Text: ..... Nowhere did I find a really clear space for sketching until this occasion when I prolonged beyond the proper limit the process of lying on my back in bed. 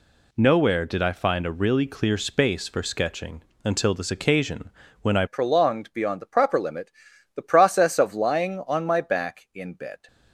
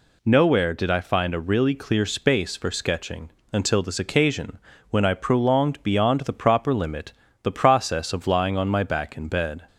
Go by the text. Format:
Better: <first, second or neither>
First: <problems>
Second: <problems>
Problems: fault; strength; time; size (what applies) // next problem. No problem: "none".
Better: second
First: pauses between "sketching" and "until"; slight; at 3.4 s; 0.24 s long // pauses between "occasion" and "when"; slight; at 4.6 s; 0.32 s long // changes voice at "prolonged"; from 5.2 s on; 4.8 s long // pauses between "limit" and "the"; at 6.9 s; 0.44 s long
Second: pauses between "sketching" and "until"; slight; at 3.2 s; 0.24 s long // pauses between "occasion" and "when"; slight; at 4.5 s; 0.32 s long // pauses between "limit" and "the"; slight; at 7.1 s; 0.28 s long